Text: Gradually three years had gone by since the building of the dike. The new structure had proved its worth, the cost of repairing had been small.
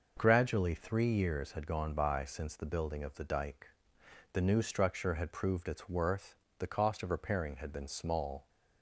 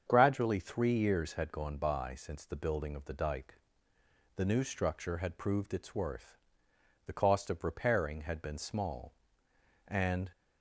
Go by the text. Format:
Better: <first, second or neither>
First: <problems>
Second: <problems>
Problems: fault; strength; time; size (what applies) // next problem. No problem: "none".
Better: first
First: none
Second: starts louder than the rest; strong; until 1.0 s; 7.5 dB // goes on to say "And"; slight; from 9.8 s on; 0.42 s long